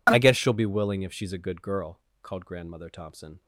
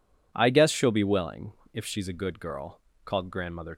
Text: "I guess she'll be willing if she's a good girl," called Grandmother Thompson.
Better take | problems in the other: first | pauses between "willing" and "if"; slight; at 1.5 s; 0.22 s long // stops before "Thompson"; at 3.7 s

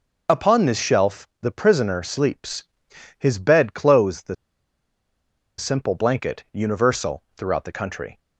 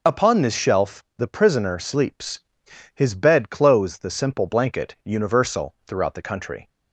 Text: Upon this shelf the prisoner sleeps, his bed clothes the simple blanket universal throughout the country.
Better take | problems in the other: second | pauses between "shelf" and "the"; slight; at 1.2 s; 0.16 s long; slight in the second // pauses between "the" and "simple"; at 4.3 s; 1.2 s long

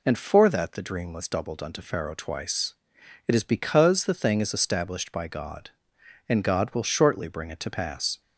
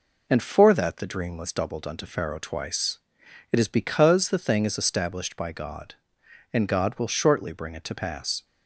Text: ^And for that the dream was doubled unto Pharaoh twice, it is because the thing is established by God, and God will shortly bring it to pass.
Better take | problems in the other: first | gets quieter; slight; throughout; 3 dB

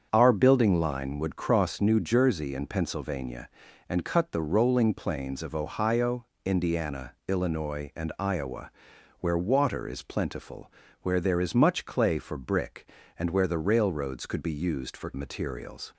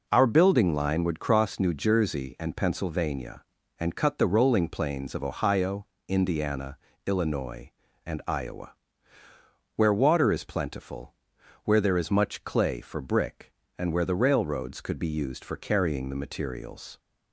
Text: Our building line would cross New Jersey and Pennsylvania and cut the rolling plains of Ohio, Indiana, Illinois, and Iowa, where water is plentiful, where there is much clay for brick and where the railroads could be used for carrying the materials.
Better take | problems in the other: second | starts louder than the rest; until 1.1 s; 7 dB // skips "carrying the"; at 15.1 s

